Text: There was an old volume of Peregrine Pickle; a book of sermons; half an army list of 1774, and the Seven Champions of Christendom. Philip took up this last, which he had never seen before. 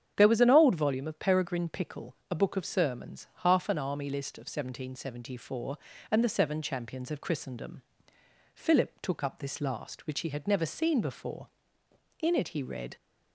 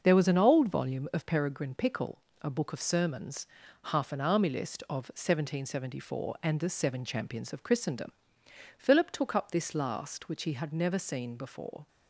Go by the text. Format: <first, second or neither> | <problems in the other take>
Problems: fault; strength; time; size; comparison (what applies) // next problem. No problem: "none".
second | starts louder than the rest; strong; until 1.1 s; 8 dB; also in the second // goes on to say "In it he read"; noticeable; from 12.2 s on; 0.74 s long